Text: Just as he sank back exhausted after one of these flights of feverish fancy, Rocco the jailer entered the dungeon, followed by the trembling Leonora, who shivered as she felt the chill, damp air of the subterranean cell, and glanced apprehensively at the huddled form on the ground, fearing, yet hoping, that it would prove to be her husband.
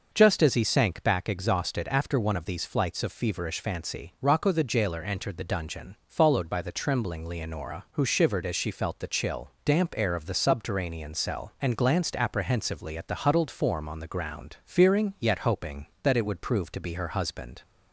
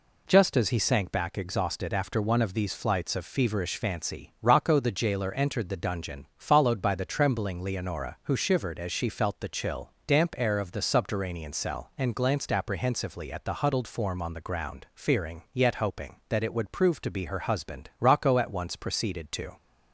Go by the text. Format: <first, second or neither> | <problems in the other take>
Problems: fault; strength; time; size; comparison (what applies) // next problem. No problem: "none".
first | goes on to say "Rocco at once proceeded to"; from 18.0 s on; 1.5 s long